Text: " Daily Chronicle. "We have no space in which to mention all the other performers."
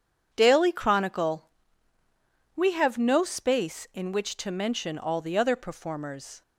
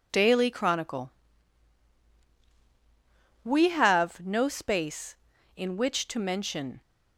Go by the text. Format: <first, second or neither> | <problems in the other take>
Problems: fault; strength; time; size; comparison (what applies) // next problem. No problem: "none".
first | stops before "all the other performers"; at 6.8 s